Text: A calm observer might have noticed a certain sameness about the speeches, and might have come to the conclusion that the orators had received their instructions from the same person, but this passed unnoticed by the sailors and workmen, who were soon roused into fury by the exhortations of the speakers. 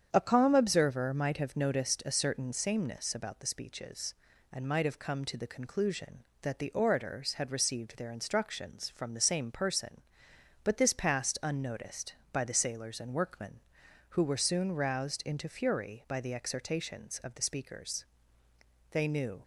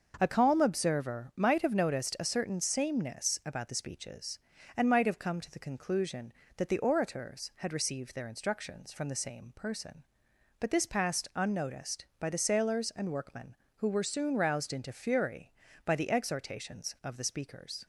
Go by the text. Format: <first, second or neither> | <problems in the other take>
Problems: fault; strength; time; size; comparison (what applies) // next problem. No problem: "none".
second | starts louder than the rest; strong; until 1.1 s; 8.5 dB; also in the second // goes on to say "They knew"; from 18.9 s on; 0.52 s long